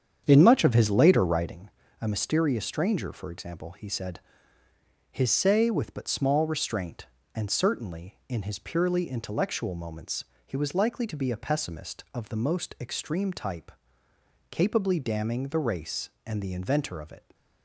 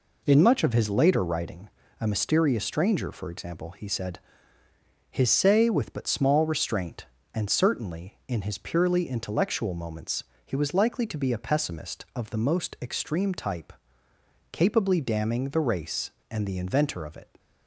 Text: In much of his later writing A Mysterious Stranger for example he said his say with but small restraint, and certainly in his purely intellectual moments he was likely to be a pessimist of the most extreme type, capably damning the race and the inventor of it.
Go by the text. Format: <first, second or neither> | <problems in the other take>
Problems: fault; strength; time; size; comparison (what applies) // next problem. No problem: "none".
second | starts louder than the rest; strong; until 1.6 s; 8 dB // pauses between "writing" and "A"; slight; at 1.6 s; 0.30 s long; slight in the second // pauses between "said" and "his"; noticeable; at 4.1 s; 0.92 s long; noticeable in the second // pauses between "moments" and "he"; slight; at 10.2 s; 0.22 s long; slight in the second